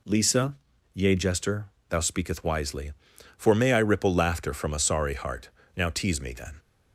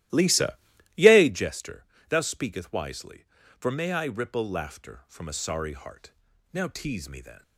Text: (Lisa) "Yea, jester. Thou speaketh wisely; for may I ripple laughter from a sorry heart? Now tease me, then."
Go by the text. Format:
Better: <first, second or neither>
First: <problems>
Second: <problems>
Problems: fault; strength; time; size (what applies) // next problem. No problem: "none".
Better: first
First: none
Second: starts louder than the rest; strong; until 1.4 s; 15 dB